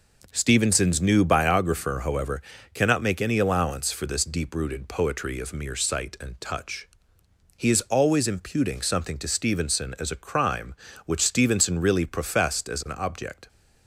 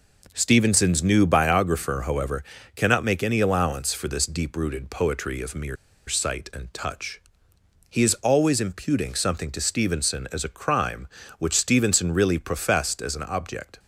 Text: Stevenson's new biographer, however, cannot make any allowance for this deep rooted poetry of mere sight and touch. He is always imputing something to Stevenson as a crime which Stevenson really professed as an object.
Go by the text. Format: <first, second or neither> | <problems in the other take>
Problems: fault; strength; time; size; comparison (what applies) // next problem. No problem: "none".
first | pauses between "mere" and "sight"; slight; at 5.7 s; 0.33 s long